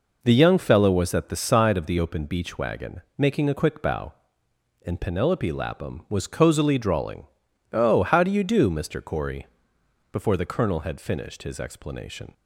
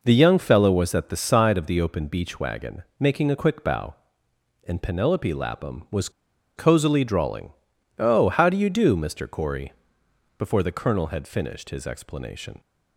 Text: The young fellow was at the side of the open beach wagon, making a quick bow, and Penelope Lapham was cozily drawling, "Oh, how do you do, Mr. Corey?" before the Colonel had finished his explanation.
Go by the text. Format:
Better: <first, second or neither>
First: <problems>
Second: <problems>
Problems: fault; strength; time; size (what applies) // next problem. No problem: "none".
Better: first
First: none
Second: pauses between "was" and "cozily"; noticeable; at 6.0 s; 0.47 s long